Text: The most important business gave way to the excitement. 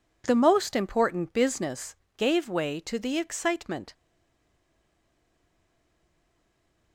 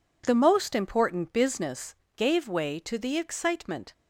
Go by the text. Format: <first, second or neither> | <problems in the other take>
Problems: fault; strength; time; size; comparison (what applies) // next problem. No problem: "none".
second | pauses between "business" and "gave"; slight; at 1.9 s; 0.22 s long; slight in the second // stays silent after the last word; strong; from 3.9 s on; 3.0 s long